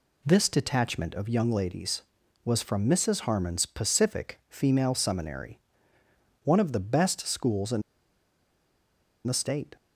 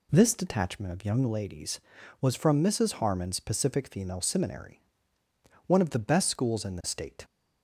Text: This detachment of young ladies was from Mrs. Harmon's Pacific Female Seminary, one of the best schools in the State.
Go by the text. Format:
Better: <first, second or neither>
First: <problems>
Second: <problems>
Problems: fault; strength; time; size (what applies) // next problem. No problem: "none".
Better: second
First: pauses between "in" and "the"; strong; at 7.8 s; 1.4 s long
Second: none